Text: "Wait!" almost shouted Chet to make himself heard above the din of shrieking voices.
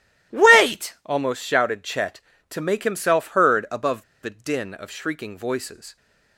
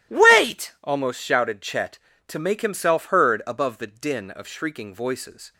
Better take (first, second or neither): second